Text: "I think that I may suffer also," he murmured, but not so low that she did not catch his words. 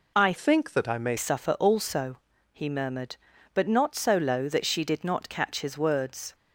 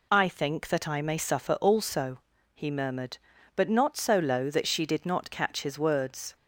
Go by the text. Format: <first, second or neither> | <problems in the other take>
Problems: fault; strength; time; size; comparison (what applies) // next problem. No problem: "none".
second | changes voice from "think" to "may"; from 0.3 to 1.1 s; 0.8 s long